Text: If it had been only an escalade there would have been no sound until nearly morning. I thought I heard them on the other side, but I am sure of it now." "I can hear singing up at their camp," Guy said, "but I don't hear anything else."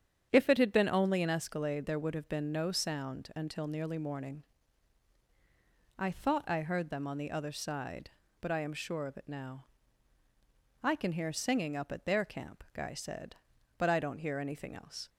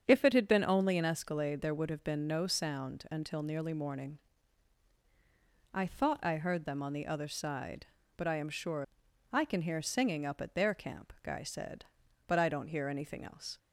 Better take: first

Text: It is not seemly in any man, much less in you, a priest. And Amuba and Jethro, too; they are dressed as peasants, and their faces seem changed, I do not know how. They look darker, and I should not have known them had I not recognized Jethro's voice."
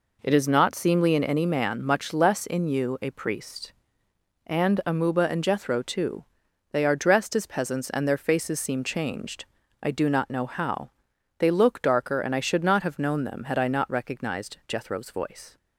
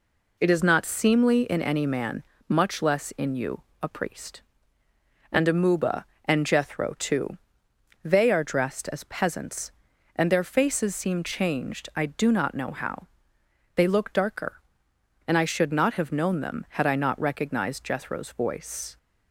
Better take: neither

